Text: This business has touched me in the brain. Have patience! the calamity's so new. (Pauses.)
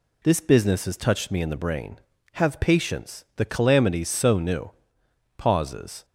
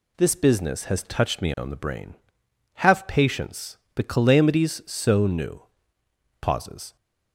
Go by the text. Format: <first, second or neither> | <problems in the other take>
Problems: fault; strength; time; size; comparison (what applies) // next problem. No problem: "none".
first | says "on" for "in"; at 1.5 s